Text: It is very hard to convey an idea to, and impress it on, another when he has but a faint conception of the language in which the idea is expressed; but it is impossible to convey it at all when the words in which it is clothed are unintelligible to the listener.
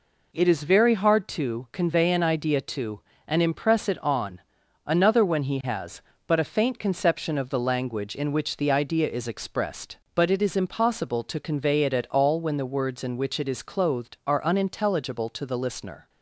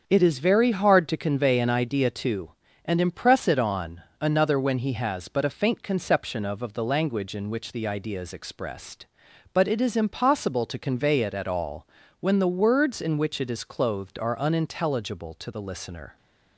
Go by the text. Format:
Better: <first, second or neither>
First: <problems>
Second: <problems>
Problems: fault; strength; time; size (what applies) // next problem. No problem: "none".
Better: first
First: none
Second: starts louder than the rest; until 1.0 s; 7 dB // says "of" twice; at 6.6 s // pauses between "all" and "when"; slight; at 11.8 s; 0.32 s long